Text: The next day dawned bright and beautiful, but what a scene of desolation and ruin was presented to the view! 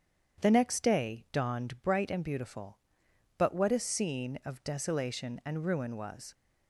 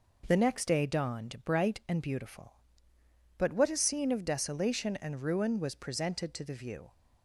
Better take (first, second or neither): second